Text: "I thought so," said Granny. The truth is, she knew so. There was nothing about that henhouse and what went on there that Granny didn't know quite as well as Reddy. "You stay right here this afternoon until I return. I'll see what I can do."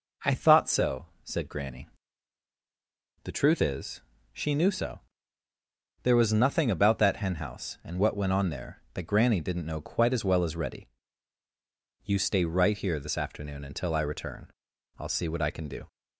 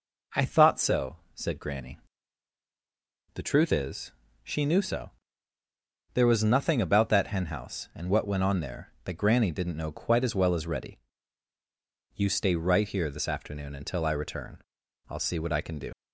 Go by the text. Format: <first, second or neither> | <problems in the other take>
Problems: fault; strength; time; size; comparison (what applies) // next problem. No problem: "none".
first | leaves "do" unfinished; at 15.9 s; 55 ms